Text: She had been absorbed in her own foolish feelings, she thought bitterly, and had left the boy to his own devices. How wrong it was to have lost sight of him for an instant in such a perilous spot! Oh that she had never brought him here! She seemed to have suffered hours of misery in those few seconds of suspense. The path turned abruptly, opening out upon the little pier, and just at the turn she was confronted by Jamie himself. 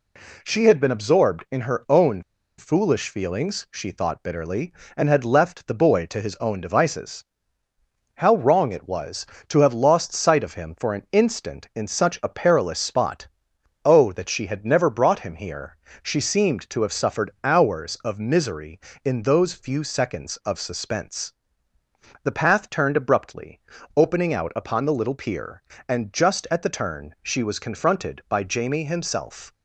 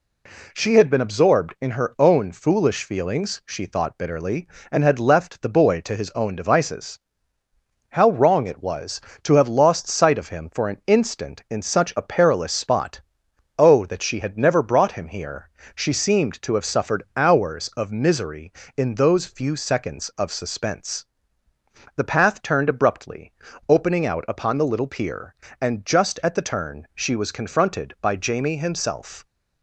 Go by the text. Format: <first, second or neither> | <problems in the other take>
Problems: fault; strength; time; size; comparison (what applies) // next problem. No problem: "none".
second | pauses between "own" and "foolish"; slight; at 2.2 s; 0.35 s long